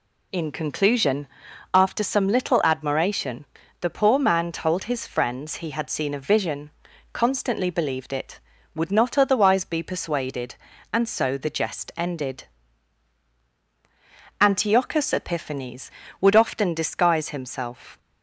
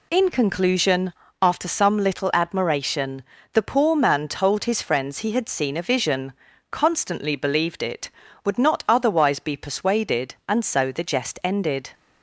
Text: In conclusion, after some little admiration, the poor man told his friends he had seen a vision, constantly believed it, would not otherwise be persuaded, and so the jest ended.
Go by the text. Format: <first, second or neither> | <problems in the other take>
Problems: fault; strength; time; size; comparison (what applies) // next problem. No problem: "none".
second | goes on to say "Antiochus Epiphanes would often disguise himself"; strong; from 14.3 s on; 3.5 s long